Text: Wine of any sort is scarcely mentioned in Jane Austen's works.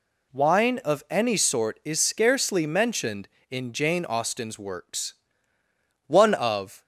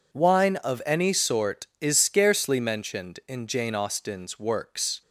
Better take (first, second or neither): second